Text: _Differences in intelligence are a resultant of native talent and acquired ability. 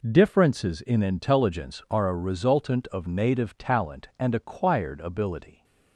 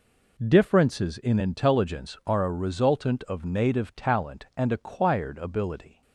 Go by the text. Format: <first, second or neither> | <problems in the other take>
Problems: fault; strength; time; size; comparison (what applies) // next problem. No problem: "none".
neither | none